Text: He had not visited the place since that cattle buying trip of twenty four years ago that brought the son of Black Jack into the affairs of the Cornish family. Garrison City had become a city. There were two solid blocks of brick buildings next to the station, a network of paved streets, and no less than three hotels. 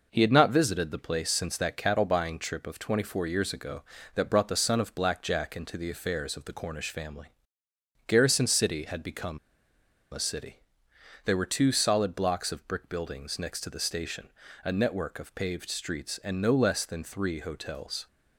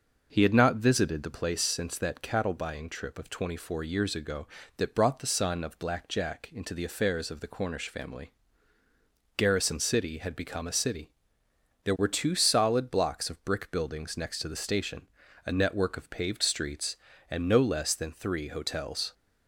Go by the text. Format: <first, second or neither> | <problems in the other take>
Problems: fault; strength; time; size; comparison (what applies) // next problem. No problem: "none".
second | pauses between "become" and "a"; noticeable; at 9.3 s; 0.74 s long